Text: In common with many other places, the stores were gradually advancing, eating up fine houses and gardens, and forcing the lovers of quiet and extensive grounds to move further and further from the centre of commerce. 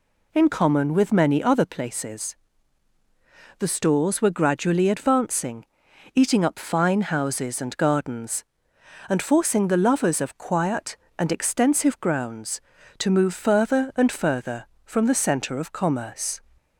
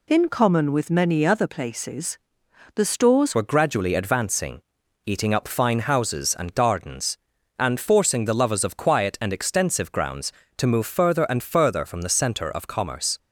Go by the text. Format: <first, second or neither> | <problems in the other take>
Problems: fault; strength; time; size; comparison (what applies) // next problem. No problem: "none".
first | changes voice at "were"; from 3.3 s on; 9.8 s long